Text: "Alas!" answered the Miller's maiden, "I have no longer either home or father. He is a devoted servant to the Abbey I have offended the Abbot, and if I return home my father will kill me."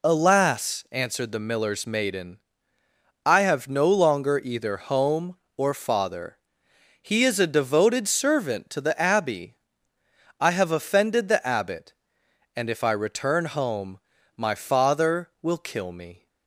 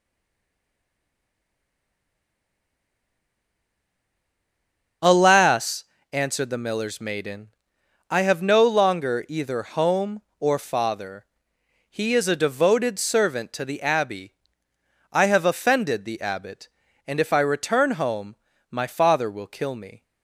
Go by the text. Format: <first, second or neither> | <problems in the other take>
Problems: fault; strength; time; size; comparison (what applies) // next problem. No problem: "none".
first | stays silent before the first word; strong; until 5.0 s; 5.0 s long // starts louder than the rest; until 6.2 s; 6.5 dB // pauses between "Abbey" and "I"; noticeable; at 14.3 s; 0.80 s long; noticeable in the first // pauses between "home" and "my"; slight; at 18.3 s; 0.34 s long; also in the first